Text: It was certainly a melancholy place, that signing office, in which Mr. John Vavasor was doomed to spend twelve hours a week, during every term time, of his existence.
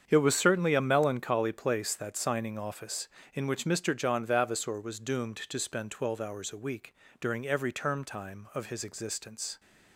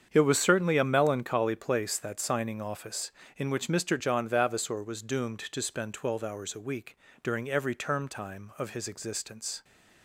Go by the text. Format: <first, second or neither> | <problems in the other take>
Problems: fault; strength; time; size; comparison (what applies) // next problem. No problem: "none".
neither | starts louder than the rest; strong; the same in both